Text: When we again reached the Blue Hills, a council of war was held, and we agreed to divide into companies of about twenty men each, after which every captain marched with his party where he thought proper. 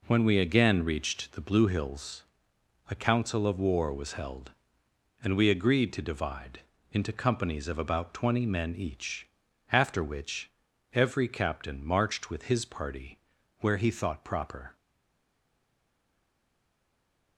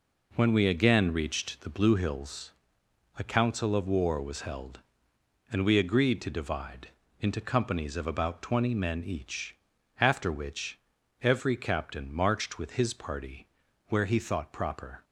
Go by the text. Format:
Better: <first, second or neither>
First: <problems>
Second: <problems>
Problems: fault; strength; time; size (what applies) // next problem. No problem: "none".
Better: second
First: pauses between "divide" and "into"; slight; at 6.5 s; 0.32 s long // pauses between "which" and "every"; at 10.5 s; 0.40 s long // pauses between "party" and "where"; at 13.1 s; 0.44 s long // stays silent after the last word; strong; from 14.7 s on; 2.6 s long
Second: pauses between "divide" and "into"; slight; at 6.8 s; 0.32 s long // pauses between "which" and "every"; at 10.7 s; 0.40 s long // pauses between "party" and "where"; at 13.4 s; 0.44 s long